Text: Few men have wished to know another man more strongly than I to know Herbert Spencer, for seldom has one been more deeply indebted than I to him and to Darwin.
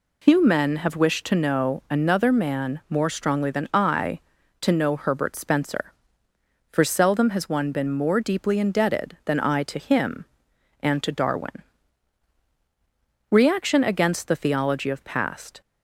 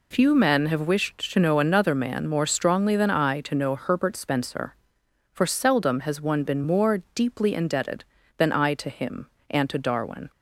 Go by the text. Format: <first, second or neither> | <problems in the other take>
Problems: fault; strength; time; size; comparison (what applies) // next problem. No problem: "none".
second | goes on to say "Reaction against the theology of past"; strong; from 13.3 s on; 2.3 s long